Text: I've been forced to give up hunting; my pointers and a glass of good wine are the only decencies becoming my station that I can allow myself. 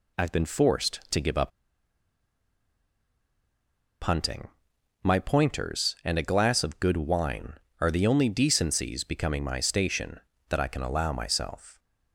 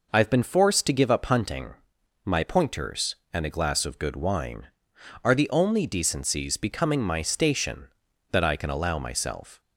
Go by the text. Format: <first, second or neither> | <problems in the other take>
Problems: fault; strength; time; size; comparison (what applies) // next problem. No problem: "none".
second | pauses between "up" and "hunting"; strong; at 1.5 s; 2.5 s long